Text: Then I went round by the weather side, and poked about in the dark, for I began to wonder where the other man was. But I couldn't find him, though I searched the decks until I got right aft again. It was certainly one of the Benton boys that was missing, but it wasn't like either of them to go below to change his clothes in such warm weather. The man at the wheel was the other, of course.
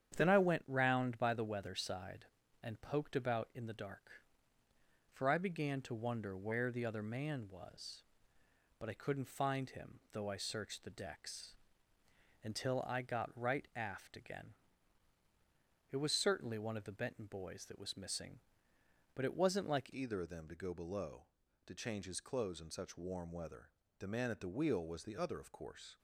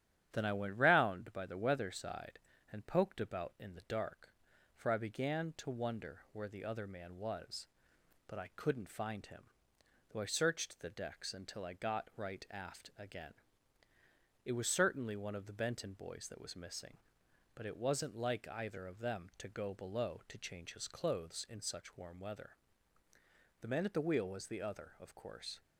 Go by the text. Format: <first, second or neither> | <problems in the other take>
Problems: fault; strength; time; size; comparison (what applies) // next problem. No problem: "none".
second | starts louder than the rest; strong; until 1.1 s; 9 dB; strong in the second // pauses between "decks" and "until"; noticeable; at 11.5 s; 0.90 s long // changes voice at "either"; from 19.9 s on; 6.0 s long